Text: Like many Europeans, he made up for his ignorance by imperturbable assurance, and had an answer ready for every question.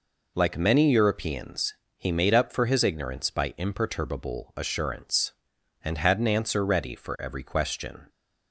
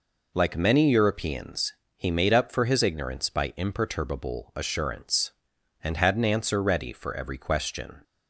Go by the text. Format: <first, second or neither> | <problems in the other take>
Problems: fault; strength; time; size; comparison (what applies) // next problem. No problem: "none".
neither | none